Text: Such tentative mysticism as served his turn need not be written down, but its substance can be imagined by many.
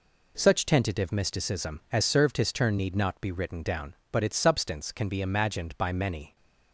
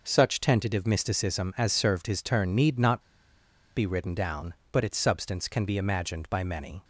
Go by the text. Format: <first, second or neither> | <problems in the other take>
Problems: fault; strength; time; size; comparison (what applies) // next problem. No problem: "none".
first | pauses between "not" and "be"; noticeable; at 3.0 s; 0.75 s long